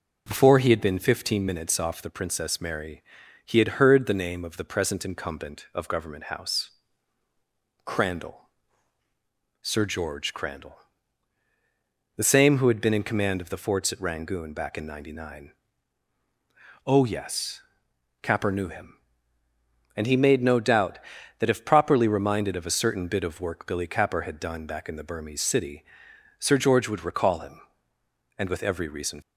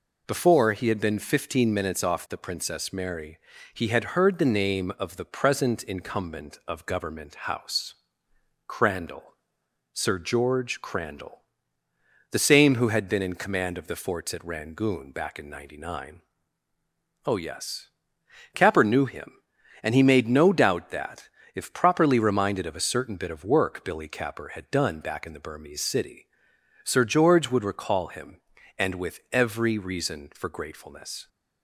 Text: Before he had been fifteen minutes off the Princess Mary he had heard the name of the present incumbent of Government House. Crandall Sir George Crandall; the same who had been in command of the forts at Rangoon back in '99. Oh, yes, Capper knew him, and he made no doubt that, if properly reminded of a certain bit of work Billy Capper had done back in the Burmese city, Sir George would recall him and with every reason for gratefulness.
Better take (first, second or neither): second